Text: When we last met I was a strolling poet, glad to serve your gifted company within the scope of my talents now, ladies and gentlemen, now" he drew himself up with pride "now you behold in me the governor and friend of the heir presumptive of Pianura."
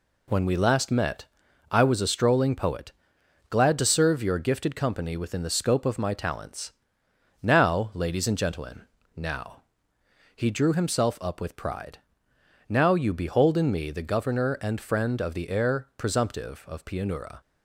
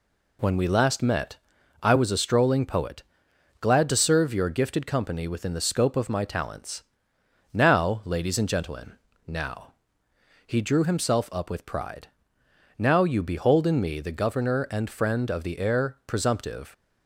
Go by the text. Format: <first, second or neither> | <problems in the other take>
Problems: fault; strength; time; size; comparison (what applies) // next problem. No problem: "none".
first | pauses between "met" and "I"; noticeable; at 1.3 s; 0.46 s long; noticeable in the first // pauses between "talents" and "now"; noticeable; at 6.8 s; 0.68 s long; noticeable in the first // pauses between "now" and "he"; noticeable; at 9.7 s; 0.72 s long; noticeable in the first // pauses between "pride" and "now"; noticeable; at 12.0 s; 0.70 s long; noticeable in the first // stops before "of Pianura"; at 16.7 s